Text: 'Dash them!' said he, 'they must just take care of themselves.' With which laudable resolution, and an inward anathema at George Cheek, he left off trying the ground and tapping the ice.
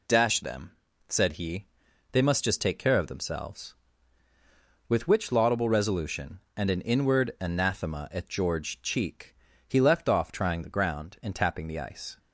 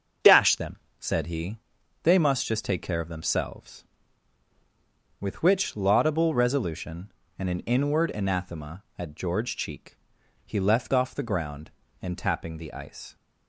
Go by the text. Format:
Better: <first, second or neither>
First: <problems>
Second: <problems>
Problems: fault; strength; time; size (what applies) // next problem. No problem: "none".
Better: first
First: none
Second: starts louder than the rest; until 1.4 s; 6.5 dB // skips "trying"; at 11.1 s